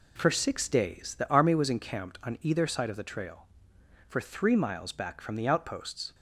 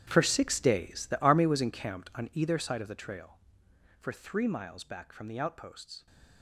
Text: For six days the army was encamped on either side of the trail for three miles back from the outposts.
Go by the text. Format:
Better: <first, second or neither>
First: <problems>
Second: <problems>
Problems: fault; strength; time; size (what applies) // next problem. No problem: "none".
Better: first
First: none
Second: gets quieter; strong; throughout; 16.5 dB